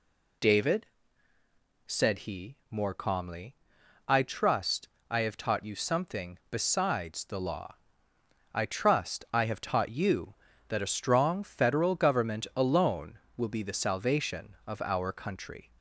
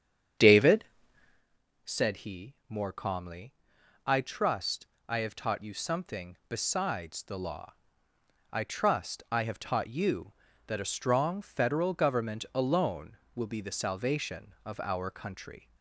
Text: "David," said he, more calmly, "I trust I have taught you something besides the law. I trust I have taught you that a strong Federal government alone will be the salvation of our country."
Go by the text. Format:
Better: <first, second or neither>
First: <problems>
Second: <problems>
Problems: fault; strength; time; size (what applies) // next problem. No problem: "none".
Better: first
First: pauses between "trust" and "I"; slight; at 4.8 s; 0.20 s long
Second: starts louder than the rest; strong; until 1.5 s; 8.5 dB // pauses between "trust" and "I"; slight; at 4.8 s; 0.20 s long